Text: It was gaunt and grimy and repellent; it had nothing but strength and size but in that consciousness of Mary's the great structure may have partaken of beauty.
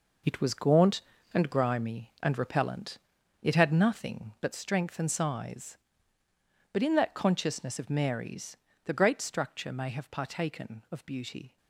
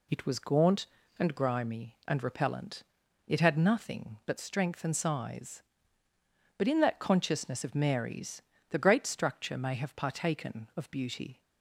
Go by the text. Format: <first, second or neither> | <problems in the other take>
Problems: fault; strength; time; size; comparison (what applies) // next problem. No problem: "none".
second | gets quieter; strong; throughout; 9.5 dB // pauses between "Mary's" and "the"; slight; at 8.5 s; 0.28 s long; slight in the second